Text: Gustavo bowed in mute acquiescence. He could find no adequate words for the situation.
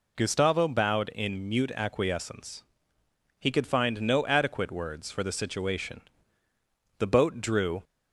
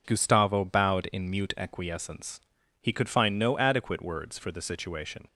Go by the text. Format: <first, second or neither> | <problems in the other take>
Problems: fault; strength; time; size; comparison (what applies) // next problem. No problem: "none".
second | goes on to say "The boat drew"; noticeable; from 6.9 s on; 0.84 s long